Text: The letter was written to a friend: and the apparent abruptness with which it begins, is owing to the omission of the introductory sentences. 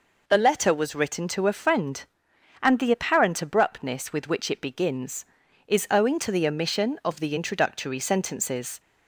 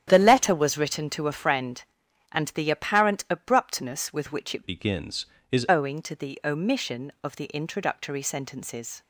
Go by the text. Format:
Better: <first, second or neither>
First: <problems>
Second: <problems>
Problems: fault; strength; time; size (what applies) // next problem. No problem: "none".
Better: first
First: none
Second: starts louder than the rest; strong; until 1.0 s; 10 dB // changes voice from "begins" to "is"; from 4.6 to 5.6 s; 1.0 s long